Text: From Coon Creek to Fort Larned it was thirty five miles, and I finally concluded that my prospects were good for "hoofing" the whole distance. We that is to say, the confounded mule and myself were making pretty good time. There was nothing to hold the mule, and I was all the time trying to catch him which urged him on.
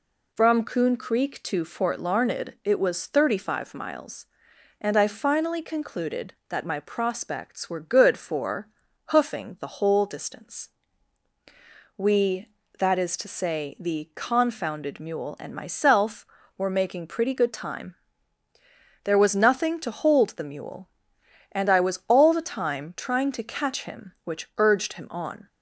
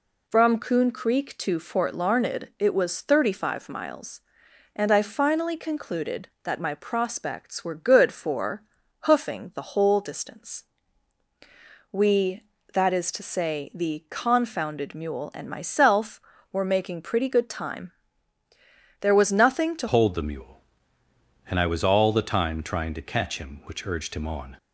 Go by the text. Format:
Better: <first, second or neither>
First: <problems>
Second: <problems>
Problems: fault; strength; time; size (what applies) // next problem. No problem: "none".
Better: first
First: pauses between "for" and "hoofing"; at 8.6 s; 0.44 s long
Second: pauses between "for" and "hoofing"; at 8.6 s; 0.44 s long // changes voice at "hold"; from 19.8 s on; 4.7 s long